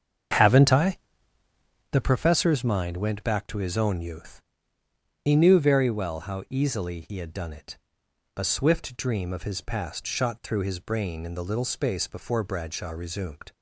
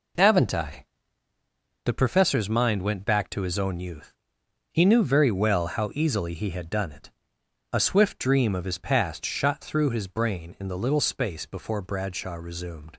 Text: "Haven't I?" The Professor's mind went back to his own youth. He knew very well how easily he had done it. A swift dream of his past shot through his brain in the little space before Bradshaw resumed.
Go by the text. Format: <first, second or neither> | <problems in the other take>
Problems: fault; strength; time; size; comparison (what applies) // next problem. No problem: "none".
second | starts louder than the rest; strong; until 2.1 s; 7.5 dB